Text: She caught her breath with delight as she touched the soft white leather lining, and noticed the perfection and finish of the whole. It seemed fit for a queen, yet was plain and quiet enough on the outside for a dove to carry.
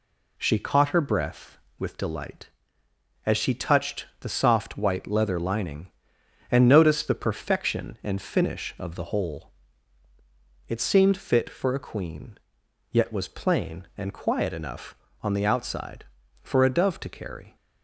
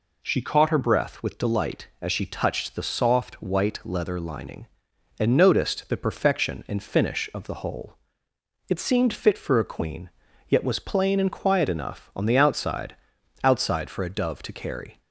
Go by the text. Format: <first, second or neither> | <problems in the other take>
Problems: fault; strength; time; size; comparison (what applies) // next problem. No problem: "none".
first | says "outside" twice; at 13.4 s